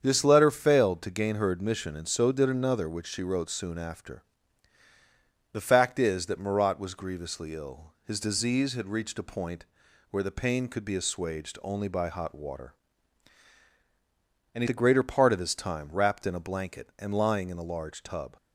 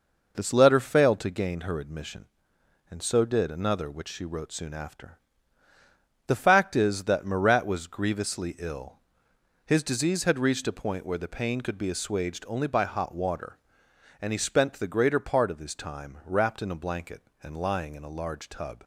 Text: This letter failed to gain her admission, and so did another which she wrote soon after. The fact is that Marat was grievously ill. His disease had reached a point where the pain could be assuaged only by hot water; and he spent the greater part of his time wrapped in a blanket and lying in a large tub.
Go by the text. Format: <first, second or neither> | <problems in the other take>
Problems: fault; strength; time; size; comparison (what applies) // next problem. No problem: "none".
second | starts louder than the rest; strong; until 1.0 s; 7.5 dB // pauses between "point" and "where"; at 9.6 s; 0.44 s long // skips "spent"; at 14.6 s